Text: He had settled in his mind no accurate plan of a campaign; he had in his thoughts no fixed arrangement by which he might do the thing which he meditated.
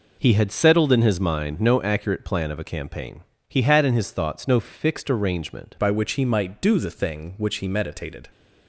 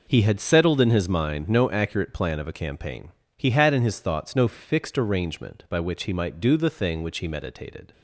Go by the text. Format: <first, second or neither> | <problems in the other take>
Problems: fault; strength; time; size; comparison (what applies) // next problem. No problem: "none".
second | changes voice at "by"; from 5.7 s on; 2.5 s long